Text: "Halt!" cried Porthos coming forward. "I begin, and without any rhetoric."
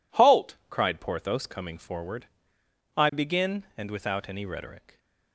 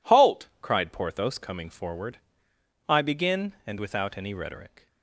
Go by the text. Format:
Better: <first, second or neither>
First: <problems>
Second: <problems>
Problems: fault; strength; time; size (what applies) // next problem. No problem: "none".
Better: neither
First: none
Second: none